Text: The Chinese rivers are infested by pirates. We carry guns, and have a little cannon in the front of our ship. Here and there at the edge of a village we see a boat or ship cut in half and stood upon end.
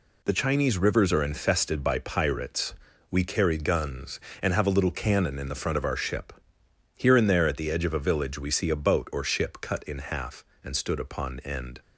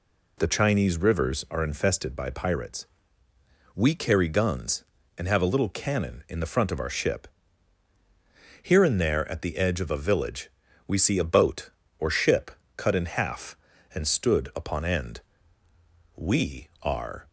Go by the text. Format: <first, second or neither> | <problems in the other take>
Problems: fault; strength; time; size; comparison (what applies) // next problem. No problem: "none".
first | pauses between "village" and "we"; at 10.4 s; 0.38 s long // pauses between "ship" and "cut"; slight; at 12.5 s; 0.26 s long // goes on to say "We are"; noticeable; from 16.1 s on; 1.1 s long